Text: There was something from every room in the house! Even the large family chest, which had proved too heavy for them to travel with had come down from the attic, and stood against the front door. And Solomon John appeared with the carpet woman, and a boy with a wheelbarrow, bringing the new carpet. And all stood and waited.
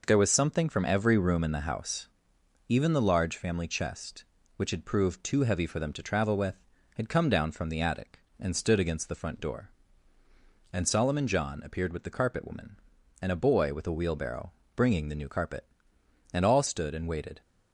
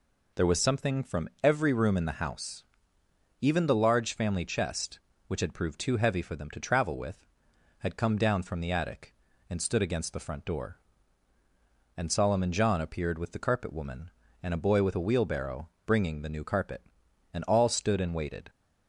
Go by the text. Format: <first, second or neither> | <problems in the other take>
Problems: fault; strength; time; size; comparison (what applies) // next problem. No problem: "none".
neither | none